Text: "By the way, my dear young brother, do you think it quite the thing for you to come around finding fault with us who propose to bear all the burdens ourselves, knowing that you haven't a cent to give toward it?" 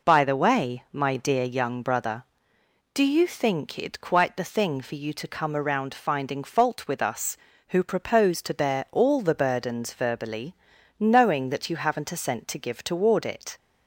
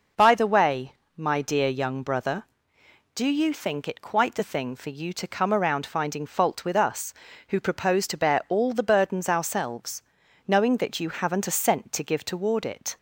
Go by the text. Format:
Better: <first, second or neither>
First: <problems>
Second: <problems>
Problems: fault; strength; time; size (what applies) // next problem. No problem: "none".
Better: second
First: says "verbally" for "ourselves"; at 9.9 s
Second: none